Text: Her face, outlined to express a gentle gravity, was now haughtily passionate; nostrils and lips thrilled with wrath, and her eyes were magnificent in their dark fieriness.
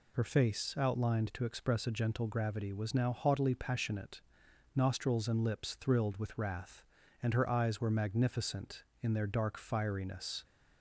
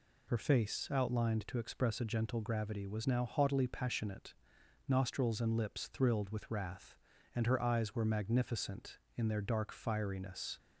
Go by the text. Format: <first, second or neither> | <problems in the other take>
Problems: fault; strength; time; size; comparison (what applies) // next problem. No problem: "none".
neither | none